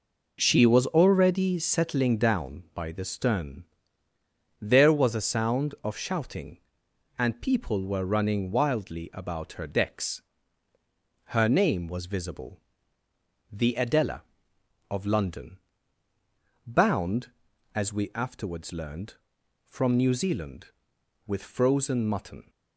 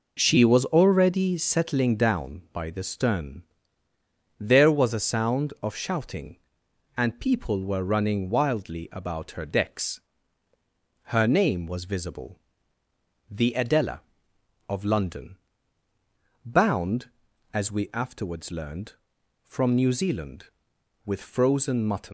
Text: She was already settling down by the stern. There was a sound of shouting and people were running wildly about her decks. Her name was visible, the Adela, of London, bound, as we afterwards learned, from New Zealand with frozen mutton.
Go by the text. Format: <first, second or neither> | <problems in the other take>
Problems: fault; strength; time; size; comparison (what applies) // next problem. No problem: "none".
first | leaves "mutton" unfinished; at 22.0 s; 150 ms